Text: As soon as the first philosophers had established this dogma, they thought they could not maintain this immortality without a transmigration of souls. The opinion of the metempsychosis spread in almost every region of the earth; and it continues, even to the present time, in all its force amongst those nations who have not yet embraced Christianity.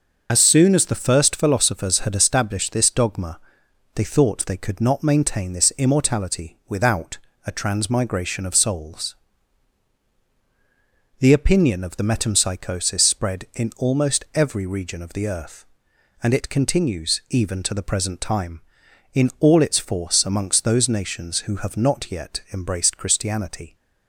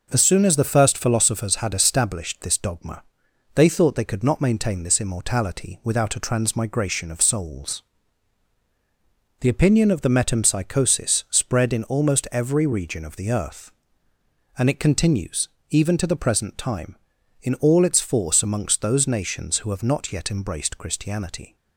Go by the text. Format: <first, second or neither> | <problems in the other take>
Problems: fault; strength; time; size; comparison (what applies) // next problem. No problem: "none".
second | loses the start of "As"; at 0.2 s; 45 ms // pauses between "without" and "a"; slight; at 7.1 s; 0.30 s long